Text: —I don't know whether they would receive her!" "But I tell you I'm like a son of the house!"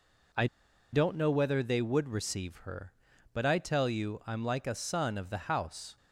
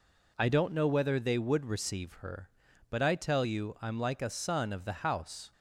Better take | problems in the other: second | pauses between "I" and "don't"; noticeable; at 0.4 s; 0.46 s long

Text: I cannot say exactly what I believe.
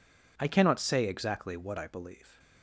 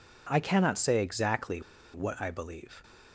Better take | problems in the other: first | pauses between "exactly" and "what"; slight; at 1.6 s; 0.32 s long

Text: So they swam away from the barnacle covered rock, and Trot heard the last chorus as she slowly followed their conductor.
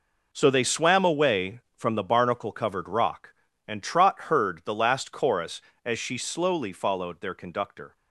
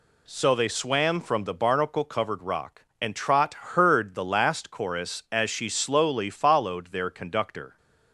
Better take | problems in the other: first | skips "away"; at 1.2 s

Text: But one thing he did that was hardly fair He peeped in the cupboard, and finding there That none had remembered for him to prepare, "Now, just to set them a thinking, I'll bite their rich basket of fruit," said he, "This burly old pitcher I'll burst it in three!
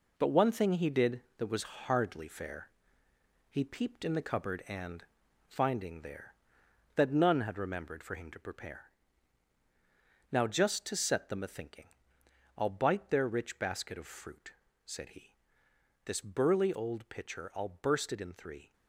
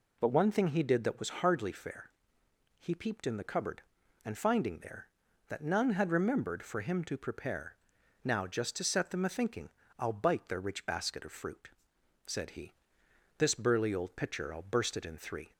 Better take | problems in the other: second | gets quieter; throughout; 6.5 dB // pauses between "fair" and "He"; noticeable; at 2.7 s; 0.80 s long; noticeable in the second // pauses between "and" and "finding"; at 5.0 s; 0.42 s long

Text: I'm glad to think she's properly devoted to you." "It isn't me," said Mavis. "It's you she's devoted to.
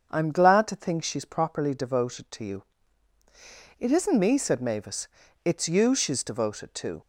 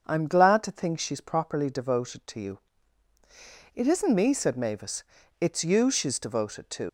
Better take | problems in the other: first | starts louder than the rest; until 1.0 s; 6.5 dB; also in the first // leaves "to" unfinished; at 6.8 s; 70 ms

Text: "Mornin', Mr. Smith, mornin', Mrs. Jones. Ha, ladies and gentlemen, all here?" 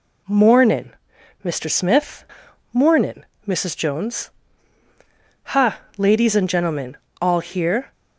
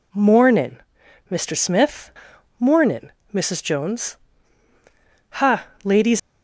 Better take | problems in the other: first | stops before "and gentlemen all here"; at 6.1 s

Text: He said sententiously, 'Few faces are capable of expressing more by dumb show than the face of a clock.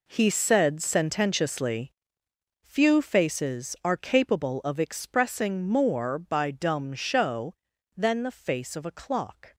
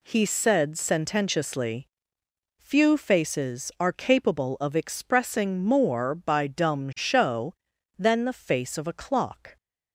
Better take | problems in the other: second | gets quieter; strong; throughout; 12 dB

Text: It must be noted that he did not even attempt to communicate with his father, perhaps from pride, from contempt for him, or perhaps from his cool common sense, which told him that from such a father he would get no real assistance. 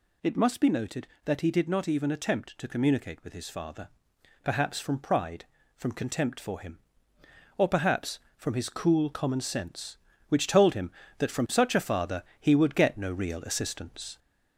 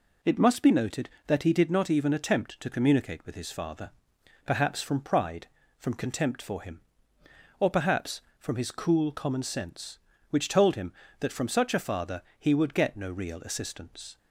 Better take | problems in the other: second | gets louder; slight; throughout; 3 dB // pauses between "father" and "he"; slight; at 12.2 s; 0.18 s long; slight in the second

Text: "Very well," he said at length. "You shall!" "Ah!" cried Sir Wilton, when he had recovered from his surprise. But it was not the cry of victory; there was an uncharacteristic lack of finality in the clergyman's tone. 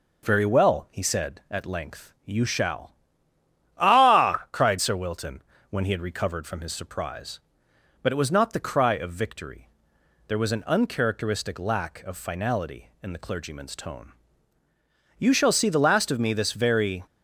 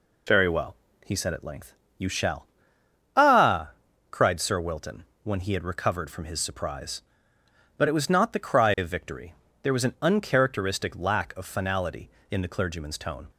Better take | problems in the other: second | goes on to say "You shall see the last of me this very"; strong; from 15.1 s on; 1.8 s long

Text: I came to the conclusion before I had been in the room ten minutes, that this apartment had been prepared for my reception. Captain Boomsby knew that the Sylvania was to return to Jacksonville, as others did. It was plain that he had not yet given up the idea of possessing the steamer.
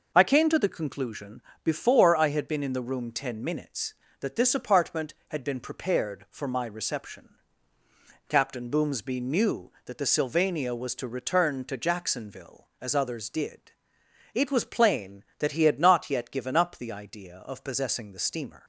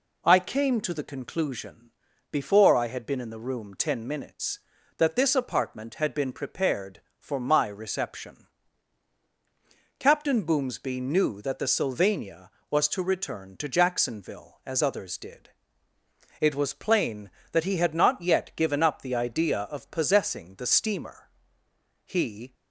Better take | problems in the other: first | pauses between "conclusion" and "before"; at 1.8 s; 0.42 s long; slight in the first // goes on to say "He"; slight; from 22.0 s on; 0.48 s long

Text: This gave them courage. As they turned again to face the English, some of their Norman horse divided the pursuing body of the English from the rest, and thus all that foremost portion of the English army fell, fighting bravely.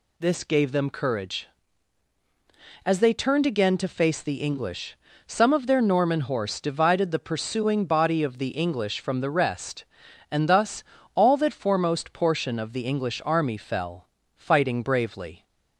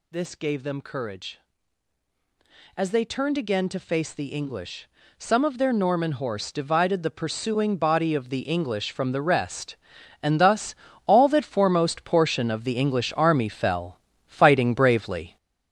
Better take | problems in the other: first | gets louder; throughout; 7 dB // pauses between "thus" and "all"; slight; at 10.7 s; 0.32 s long; slight in the first

